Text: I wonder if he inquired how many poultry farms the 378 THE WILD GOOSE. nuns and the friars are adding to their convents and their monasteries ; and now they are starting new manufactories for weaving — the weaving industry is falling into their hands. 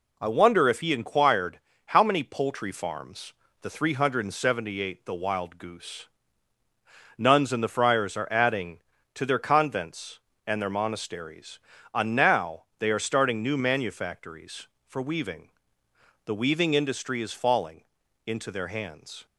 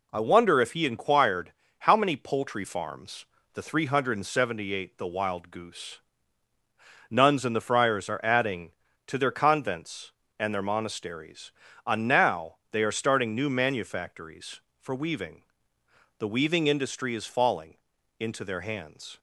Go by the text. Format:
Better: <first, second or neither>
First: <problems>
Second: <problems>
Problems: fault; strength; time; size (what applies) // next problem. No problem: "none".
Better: neither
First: pauses between "inquired" and "how"; slight; at 1.6 s; 0.26 s long // pauses between "farms" and "the"; slight; at 3.3 s; 0.26 s long // pauses between "now" and "they"; slight; at 12.6 s; 0.16 s long // pauses between "falling" and "into"; at 17.8 s; 0.42 s long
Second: pauses between "inquired" and "how"; slight; at 1.5 s; 0.26 s long // pauses between "farms" and "the"; slight; at 3.2 s; 0.26 s long // pauses between "now" and "they"; slight; at 12.5 s; 0.16 s long // pauses between "falling" and "into"; at 17.7 s; 0.42 s long